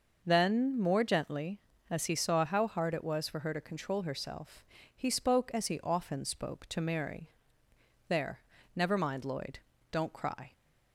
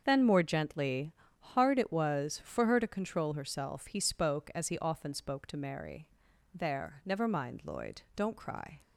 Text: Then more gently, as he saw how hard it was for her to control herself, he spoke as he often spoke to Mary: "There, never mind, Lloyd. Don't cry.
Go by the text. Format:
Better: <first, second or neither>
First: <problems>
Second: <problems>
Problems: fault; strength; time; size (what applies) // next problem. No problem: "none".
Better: first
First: none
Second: starts louder than the rest; until 1.0 s; 7 dB // skips "as he saw how"; at 1.2 s